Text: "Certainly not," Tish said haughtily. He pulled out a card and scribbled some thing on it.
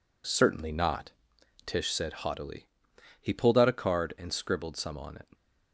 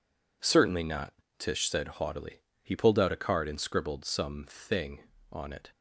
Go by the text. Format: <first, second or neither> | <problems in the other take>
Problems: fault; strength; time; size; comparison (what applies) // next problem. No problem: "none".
second | skips "thing"; at 4.9 s